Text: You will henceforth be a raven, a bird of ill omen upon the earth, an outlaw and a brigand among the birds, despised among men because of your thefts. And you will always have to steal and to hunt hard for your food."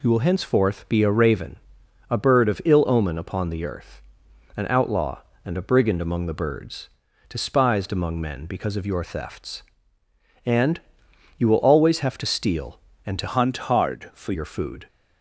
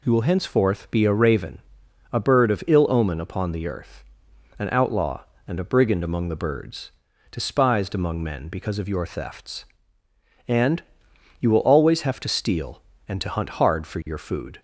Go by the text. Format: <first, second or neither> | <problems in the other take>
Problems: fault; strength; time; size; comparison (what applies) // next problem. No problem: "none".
second | pauses between "And" and "you"; noticeable; at 10.7 s; 0.58 s long; noticeable in the second // changes voice from "hunt" to "for"; from 13.2 to 14.3 s; 1.1 s long